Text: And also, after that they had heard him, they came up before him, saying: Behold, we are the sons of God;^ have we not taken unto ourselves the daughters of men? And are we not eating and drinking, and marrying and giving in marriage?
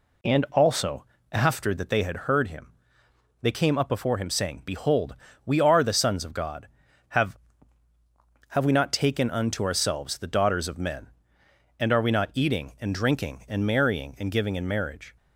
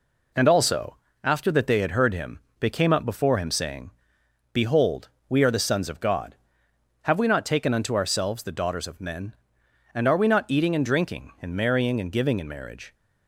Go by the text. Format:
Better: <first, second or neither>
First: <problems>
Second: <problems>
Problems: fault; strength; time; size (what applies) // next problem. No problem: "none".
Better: second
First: says "have" twice; at 8.4 s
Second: none